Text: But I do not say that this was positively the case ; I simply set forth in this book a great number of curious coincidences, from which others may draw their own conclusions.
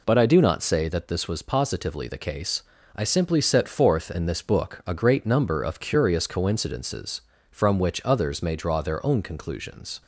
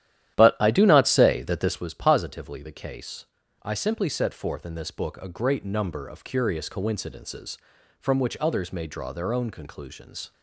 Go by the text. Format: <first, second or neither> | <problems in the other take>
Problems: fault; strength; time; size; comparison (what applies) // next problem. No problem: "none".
first | starts louder than the rest; strong; until 1.9 s; 11.5 dB